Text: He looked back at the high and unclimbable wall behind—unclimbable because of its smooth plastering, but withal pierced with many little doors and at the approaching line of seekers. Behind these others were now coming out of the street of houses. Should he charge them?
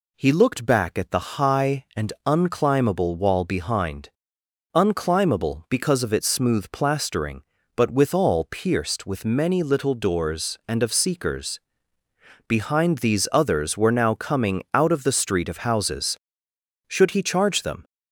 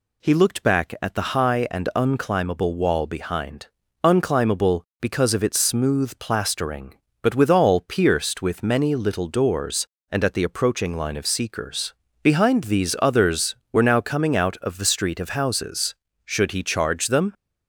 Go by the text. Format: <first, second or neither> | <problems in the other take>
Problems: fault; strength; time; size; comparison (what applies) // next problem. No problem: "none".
second | skips "at the approaching line"; at 10.8 s